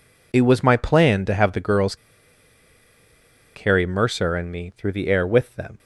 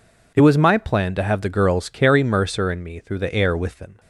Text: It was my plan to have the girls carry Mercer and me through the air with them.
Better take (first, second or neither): second